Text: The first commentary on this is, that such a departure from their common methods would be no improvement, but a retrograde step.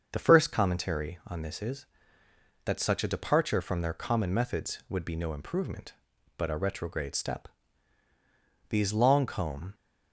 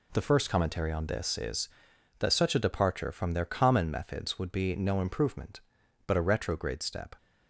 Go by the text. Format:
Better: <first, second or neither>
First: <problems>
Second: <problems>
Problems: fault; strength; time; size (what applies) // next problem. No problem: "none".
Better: second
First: starts louder than the rest; until 1.1 s; 6.5 dB // goes on to say "These long comb"; noticeable; from 8.6 s on; 1.0 s long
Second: none